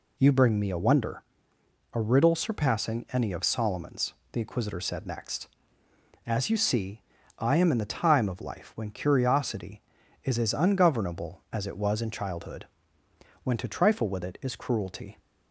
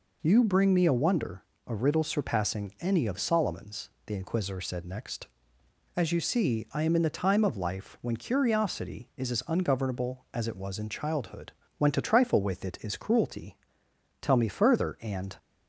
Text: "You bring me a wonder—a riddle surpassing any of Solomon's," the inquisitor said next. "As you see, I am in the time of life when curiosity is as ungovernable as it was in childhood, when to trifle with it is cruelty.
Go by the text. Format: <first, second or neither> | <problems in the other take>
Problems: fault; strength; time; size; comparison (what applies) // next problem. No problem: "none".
first | goes on to say "Tell me further and"; noticeable; from 14.2 s on; 1.1 s long